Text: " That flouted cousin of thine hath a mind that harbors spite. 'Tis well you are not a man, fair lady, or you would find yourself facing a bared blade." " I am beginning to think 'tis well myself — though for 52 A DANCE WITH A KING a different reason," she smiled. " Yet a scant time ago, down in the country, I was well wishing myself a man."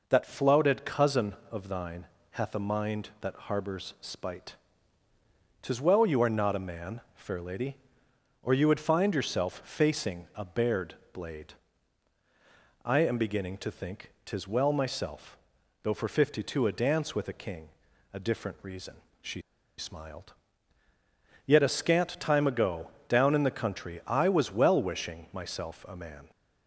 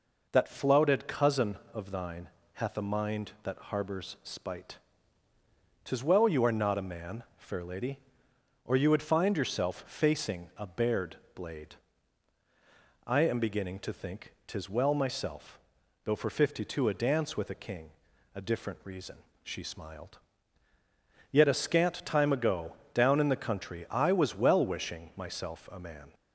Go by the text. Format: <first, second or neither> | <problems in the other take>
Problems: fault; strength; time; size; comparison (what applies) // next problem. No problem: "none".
second | pauses between "thine" and "hath"; slight; at 2.0 s; 0.26 s long; slight in the second // pauses between "bared" and "blade"; slight; at 10.9 s; 0.18 s long; slight in the second // pauses between "KING" and "a"; at 17.6 s; 0.42 s long; also in the second // pauses between "she" and "smiled"; at 19.4 s; 0.36 s long